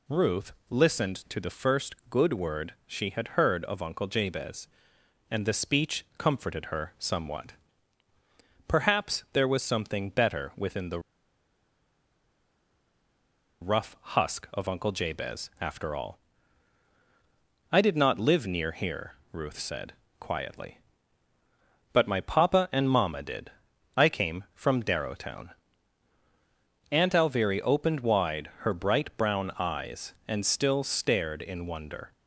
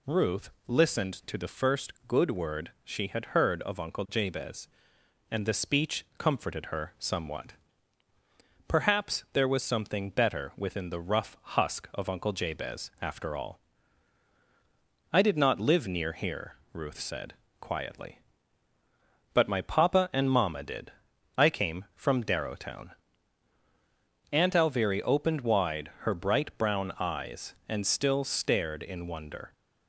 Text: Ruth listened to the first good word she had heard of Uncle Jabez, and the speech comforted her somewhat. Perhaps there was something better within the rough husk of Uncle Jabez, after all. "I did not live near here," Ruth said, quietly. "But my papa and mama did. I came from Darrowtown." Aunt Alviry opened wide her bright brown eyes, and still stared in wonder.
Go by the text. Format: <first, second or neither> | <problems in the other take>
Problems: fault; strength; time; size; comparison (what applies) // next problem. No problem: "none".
second | pauses between "Ruth" and "listened"; slight; at 0.5 s; 0.16 s long; slight in the second // pauses between "first" and "good"; slight; at 1.9 s; 0.16 s long; slight in the second // pauses between "the" and "rough"; strong; at 11.0 s; 2.6 s long